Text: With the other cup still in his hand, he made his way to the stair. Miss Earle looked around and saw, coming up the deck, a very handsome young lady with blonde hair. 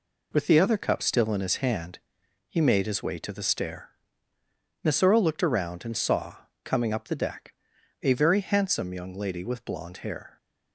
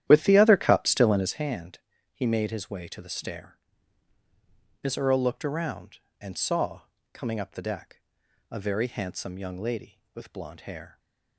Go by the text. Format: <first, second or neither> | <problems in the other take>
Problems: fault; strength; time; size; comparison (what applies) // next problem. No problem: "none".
first | starts louder than the rest; strong; until 1.3 s; 11.5 dB // stays silent after the last word; slight; from 10.8 s on; 0.5 s long